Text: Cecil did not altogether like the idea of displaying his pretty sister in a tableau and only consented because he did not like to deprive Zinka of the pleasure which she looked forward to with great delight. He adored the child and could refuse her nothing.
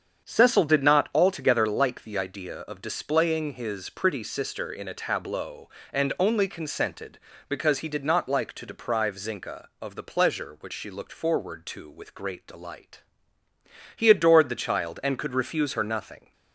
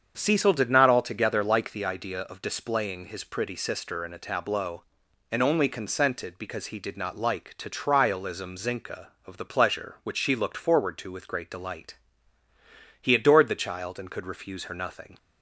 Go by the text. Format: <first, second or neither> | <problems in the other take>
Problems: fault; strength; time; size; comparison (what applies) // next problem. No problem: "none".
first | starts louder than the rest; strong; until 1.1 s; 7.5 dB; strong in the first // says "trialism" for "deprive"; at 7.6 s